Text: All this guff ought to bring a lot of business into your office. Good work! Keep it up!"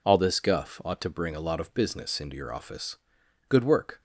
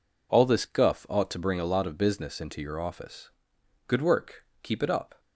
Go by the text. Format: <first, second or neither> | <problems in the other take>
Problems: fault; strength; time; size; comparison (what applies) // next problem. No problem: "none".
second | stops before "Keep it up"; at 3.9 s